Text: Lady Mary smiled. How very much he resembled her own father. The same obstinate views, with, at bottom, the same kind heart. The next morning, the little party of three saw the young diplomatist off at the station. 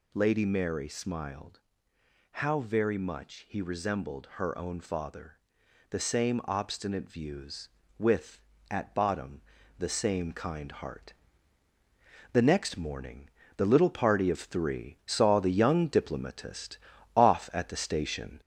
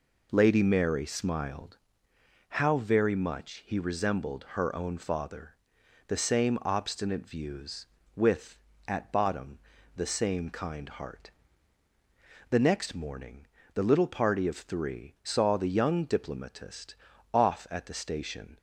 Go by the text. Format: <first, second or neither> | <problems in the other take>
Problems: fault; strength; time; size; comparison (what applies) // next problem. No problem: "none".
second | gets louder; slight; throughout; 2.5 dB // pauses between "diplomatist" and "off"; at 16.7 s; 0.38 s long; also in the second